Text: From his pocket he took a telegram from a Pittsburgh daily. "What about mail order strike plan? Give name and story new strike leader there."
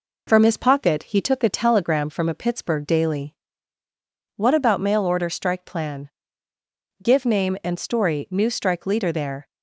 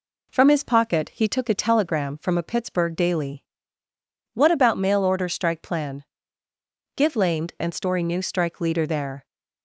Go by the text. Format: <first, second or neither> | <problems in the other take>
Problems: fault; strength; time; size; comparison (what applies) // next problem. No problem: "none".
first | says "lamed" for "name"; at 7.1 s